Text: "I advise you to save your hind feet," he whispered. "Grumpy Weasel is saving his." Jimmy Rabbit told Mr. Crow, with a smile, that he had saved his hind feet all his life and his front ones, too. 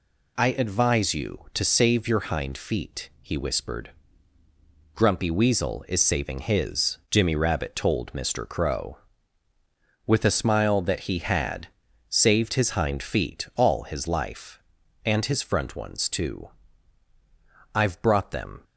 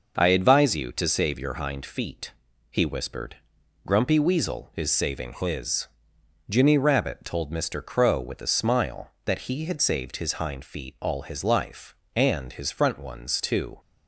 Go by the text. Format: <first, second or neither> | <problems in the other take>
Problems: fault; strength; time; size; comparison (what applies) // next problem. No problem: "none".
second | pauses between "had" and "saved"; at 11.6 s; 0.40 s long // goes on to say "I've brought them"; noticeable; from 17.7 s on; 0.88 s long